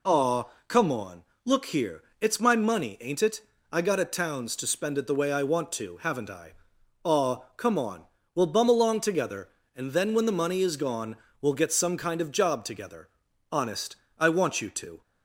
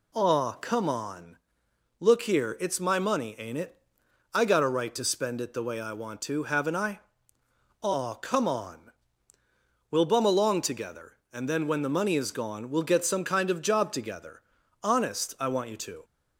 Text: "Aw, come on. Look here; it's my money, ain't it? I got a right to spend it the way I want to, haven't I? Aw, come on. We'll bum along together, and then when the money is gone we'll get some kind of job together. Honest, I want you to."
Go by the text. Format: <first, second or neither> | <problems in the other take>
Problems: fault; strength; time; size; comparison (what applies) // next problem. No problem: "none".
second | says "towns" for "right"; at 4.0 s // pauses between "gone" and "we'll"; slight; at 11.1 s; 0.24 s long